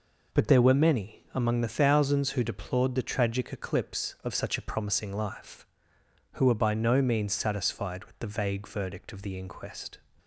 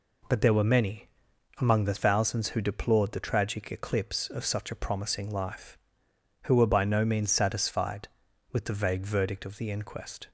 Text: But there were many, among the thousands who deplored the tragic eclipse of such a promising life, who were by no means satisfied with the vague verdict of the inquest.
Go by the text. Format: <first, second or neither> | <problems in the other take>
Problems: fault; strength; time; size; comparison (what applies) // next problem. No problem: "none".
neither | none